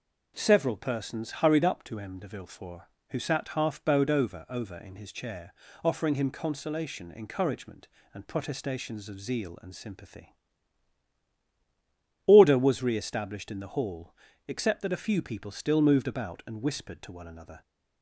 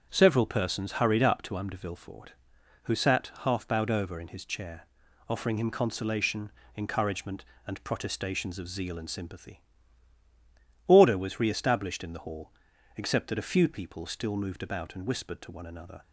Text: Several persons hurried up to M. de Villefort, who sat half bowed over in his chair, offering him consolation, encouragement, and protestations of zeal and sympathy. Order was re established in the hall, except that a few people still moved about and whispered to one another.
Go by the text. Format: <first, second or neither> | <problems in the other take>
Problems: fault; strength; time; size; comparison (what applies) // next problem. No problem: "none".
second | says "over" twice; at 4.4 s